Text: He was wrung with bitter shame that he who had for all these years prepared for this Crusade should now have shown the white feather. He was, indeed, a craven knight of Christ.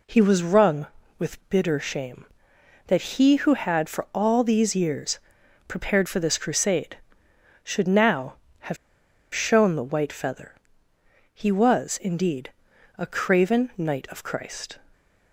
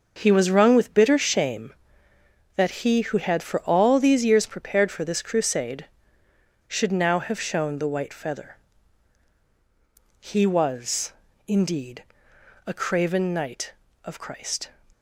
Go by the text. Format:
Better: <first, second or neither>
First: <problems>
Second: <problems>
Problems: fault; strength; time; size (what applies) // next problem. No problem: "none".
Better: second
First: pauses between "years" and "prepared"; noticeable; at 5.1 s; 0.50 s long // pauses between "have" and "shown"; noticeable; at 8.7 s; 0.58 s long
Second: none